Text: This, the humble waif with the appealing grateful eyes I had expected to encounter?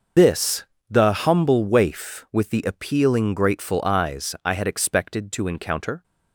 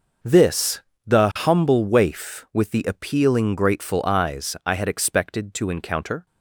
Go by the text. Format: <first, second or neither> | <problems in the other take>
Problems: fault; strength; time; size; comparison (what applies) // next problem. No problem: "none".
second | loses the start of "This"; at 0.1 s; 95 ms